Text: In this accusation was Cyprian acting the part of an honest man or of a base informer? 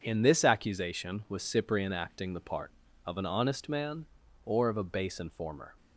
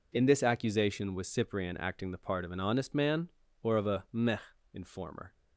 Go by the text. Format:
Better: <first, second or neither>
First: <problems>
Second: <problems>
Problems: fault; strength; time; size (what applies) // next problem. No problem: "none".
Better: first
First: none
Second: says "meh" for "base"; at 4.1 s